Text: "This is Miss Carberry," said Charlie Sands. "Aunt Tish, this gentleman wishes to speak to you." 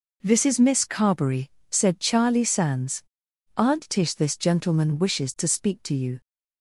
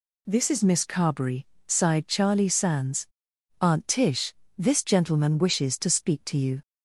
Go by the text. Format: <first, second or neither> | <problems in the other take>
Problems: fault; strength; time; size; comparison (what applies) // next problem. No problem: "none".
first | says "sighed" for "said"; at 1.6 s